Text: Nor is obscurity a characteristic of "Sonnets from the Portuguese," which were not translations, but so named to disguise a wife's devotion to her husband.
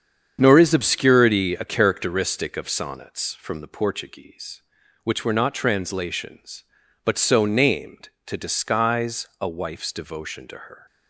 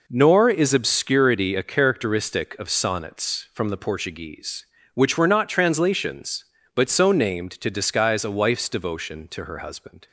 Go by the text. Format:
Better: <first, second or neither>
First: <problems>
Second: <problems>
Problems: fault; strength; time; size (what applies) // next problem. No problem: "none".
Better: second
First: starts louder than the rest; strong; until 1.4 s; 7.5 dB // stops before "husband"; at 10.8 s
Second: none